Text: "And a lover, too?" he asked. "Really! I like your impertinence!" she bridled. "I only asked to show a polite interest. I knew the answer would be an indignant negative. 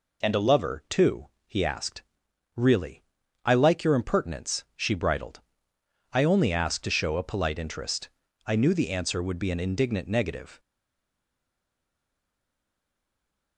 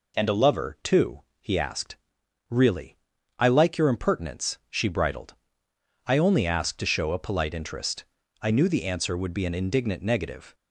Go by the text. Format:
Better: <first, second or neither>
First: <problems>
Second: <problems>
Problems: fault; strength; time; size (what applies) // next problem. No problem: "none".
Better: second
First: stays silent after the last word; strong; from 10.5 s on; 3.0 s long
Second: none